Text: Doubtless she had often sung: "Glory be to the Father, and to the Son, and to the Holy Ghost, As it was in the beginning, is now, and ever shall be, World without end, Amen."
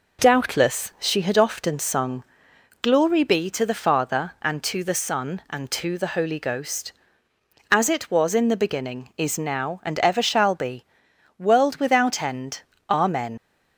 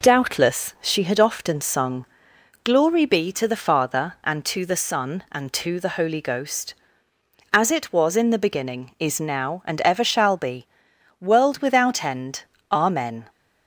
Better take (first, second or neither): second